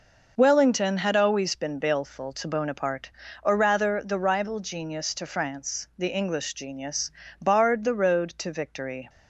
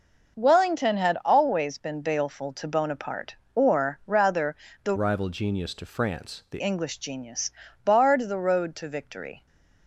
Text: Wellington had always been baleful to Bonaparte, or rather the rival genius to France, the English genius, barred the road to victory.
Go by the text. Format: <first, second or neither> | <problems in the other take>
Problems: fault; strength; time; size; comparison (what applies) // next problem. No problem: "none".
first | pauses between "rather" and "the"; slight; at 4.5 s; 0.30 s long // changes voice from "rival" to "the"; from 4.9 to 6.6 s; 1.7 s long